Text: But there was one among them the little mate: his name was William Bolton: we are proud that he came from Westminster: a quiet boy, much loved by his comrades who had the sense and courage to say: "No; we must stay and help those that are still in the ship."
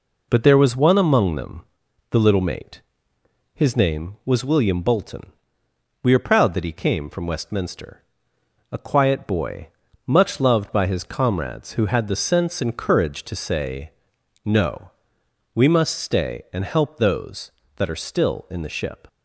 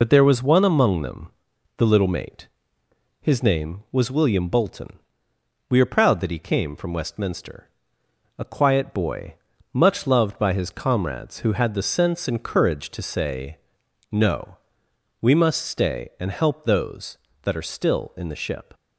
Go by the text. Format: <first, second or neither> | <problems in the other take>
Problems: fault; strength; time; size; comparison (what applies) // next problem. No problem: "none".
first | loses the start of "But"; at 0.0 s; 50 ms // pauses between "them" and "the"; noticeable; at 1.2 s; 0.48 s long; noticeable in the first